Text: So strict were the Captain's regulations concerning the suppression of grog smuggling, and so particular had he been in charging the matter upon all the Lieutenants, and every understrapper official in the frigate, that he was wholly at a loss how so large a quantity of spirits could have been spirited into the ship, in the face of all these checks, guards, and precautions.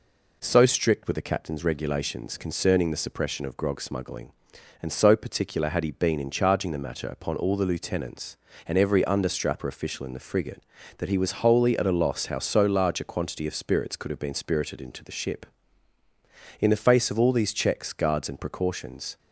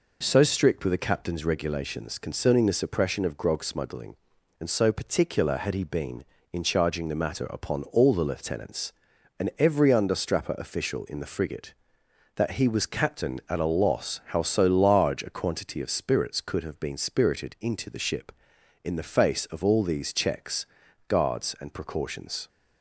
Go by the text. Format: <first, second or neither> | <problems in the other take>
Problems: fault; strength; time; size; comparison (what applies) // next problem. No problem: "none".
first | says "captain" for "wholly"; at 12.8 s